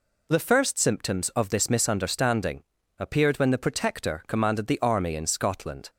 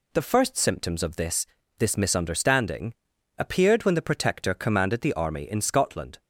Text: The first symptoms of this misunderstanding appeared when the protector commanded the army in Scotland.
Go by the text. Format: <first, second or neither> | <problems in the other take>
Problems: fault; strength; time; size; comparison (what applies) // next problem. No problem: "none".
first | says "this" twice; at 1.7 s // pauses between "misunderstanding" and "appeared"; at 2.9 s; 0.44 s long; slight in the first